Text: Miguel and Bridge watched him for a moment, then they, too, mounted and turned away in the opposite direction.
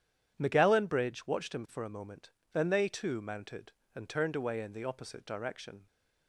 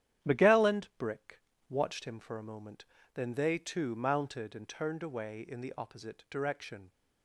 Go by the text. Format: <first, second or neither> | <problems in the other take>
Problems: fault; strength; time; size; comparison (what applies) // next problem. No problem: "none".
first | starts louder than the rest; strong; until 1.3 s; 10.5 dB; strong in the first // says "Brick" for "Bridge"; at 0.9 s